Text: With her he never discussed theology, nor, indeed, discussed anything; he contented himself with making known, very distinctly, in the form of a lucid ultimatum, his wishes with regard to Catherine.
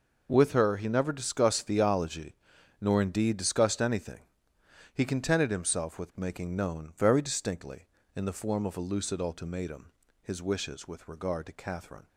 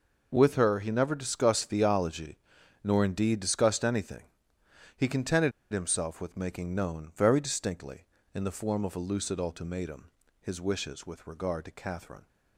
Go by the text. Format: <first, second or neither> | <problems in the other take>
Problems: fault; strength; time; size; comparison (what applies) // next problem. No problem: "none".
first | pauses between "contented" and "himself"; slight; at 5.5 s; 0.21 s long